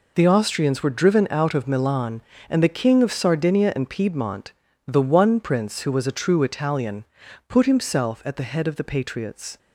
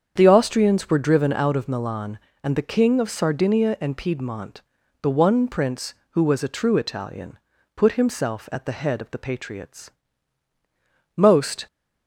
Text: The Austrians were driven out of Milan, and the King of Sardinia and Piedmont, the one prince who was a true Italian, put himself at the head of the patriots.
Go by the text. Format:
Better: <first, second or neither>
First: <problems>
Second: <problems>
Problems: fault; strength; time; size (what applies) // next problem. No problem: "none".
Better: first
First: none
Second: starts louder than the rest; strong; until 1.1 s; 7.5 dB // goes on to say "Most"; from 11.1 s on; 0.52 s long